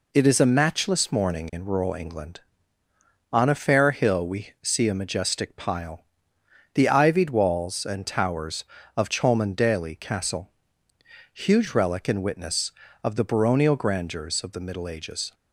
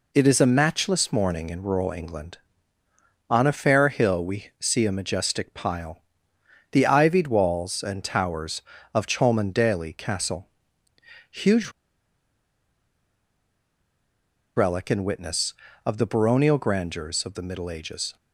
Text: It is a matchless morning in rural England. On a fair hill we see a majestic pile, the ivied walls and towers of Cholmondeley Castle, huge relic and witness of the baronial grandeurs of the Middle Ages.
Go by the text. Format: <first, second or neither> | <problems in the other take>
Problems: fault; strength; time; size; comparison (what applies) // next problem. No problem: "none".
first | pauses between "huge" and "relic"; strong; at 11.7 s; 2.8 s long